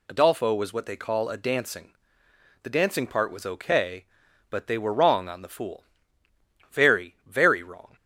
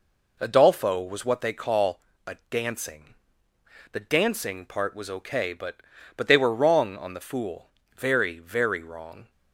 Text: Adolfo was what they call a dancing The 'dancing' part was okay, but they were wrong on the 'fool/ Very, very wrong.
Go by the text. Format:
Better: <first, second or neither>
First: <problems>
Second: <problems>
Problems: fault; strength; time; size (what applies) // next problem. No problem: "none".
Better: first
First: pauses between "dancing" and "The"; noticeable; at 1.9 s; 0.70 s long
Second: pauses between "call" and "a"; slight; at 1.9 s; 0.28 s long // pauses between "a" and "dancing"; slight; at 2.3 s; 0.16 s long // pauses between "dancing" and "The"; noticeable; at 3.1 s; 0.76 s long // says "but" twice; at 6.1 s